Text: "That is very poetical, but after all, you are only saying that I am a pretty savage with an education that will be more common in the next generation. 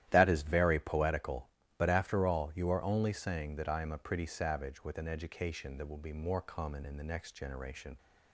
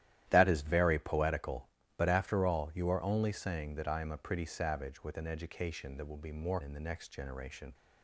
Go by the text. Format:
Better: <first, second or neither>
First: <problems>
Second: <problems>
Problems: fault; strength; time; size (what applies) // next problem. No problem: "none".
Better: first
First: starts louder than the rest; strong; until 1.1 s; 12.5 dB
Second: starts louder than the rest; strong; until 1.3 s; 12.5 dB // skips "common"; at 6.6 s